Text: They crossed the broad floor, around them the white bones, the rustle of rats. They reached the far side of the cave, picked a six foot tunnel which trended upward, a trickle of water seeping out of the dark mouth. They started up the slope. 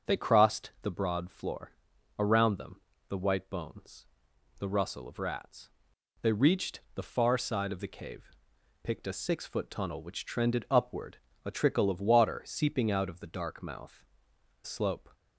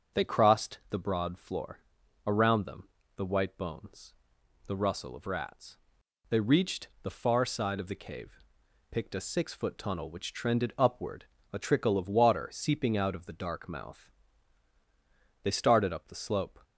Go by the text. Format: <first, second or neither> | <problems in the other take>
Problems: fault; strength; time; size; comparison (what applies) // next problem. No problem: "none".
second | starts louder than the rest; until 1.2 s; 6 dB; also in the second // pauses between "them" and "the"; slight; at 2.7 s; 0.28 s long; slight in the second // skips "They started up the"; at 14.3 s